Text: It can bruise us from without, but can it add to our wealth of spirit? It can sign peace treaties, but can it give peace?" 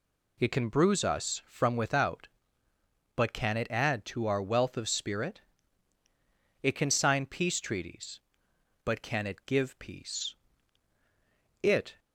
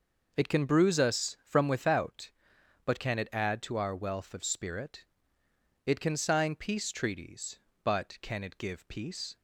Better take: second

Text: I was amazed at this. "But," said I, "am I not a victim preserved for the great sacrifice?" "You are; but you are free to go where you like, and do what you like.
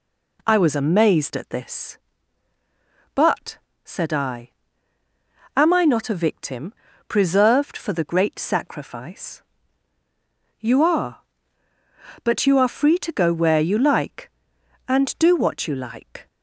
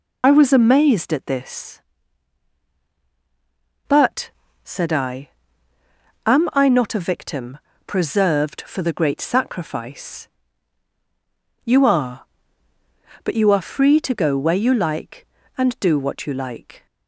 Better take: first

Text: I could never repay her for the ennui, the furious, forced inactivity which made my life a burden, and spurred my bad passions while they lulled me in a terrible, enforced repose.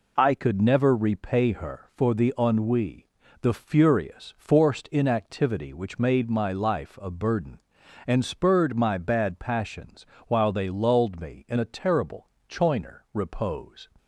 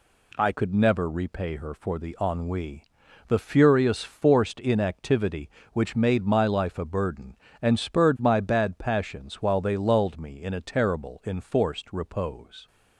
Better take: second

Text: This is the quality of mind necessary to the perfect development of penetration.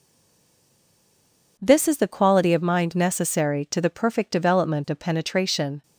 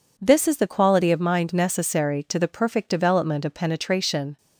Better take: second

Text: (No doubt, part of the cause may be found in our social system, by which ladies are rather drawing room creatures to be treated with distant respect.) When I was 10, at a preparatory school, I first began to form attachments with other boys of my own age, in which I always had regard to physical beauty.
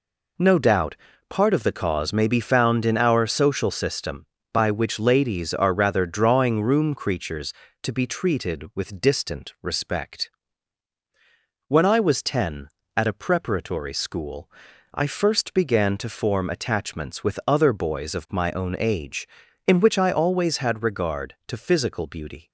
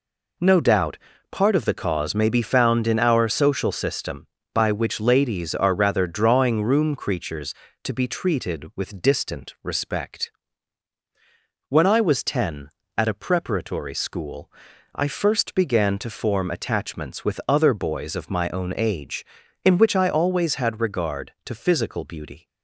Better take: neither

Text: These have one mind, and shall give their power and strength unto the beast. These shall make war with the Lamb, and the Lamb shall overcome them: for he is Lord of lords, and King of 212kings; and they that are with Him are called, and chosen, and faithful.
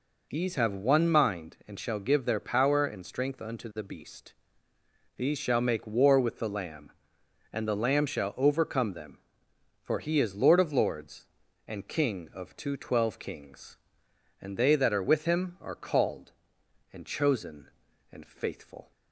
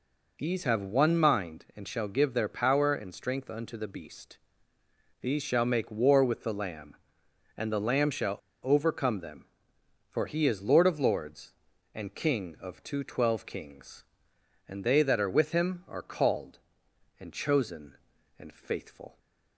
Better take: first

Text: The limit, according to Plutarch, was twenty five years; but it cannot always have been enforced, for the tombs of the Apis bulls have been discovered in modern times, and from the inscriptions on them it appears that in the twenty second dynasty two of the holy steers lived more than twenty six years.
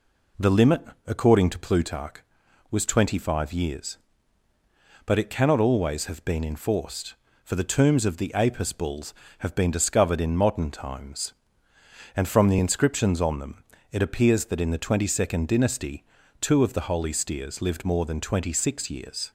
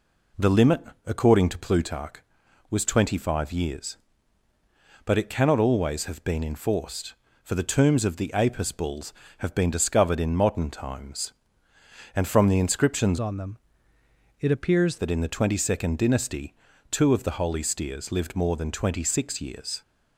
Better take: first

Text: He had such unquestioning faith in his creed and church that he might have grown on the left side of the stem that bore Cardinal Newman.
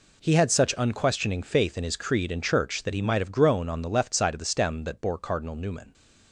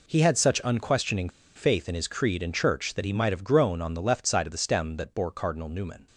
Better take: first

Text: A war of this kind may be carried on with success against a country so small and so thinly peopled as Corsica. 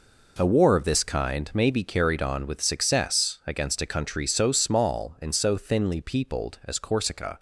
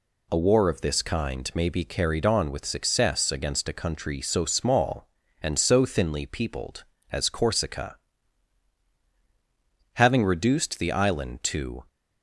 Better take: first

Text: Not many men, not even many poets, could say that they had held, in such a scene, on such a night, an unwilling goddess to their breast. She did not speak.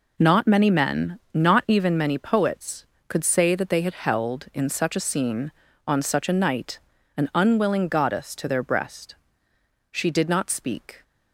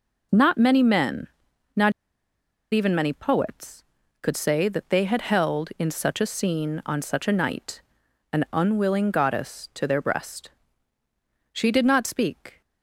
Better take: first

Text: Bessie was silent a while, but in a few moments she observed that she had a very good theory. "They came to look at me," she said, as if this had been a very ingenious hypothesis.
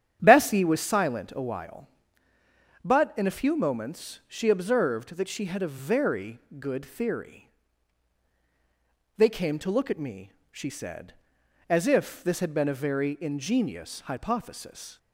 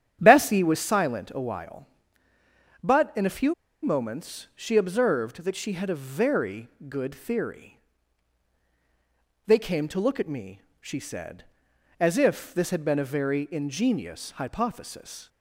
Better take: first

